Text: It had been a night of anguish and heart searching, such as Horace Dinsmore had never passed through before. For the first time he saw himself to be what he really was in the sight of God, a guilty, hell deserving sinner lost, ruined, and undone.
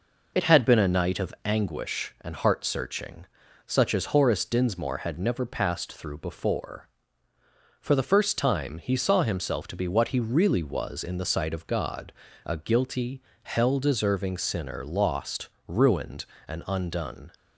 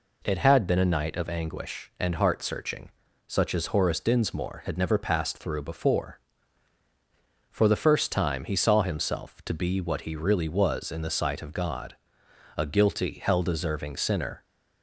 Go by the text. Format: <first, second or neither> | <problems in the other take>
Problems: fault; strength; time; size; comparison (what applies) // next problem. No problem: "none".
first | stops before "lost ruined and undone"; at 14.4 s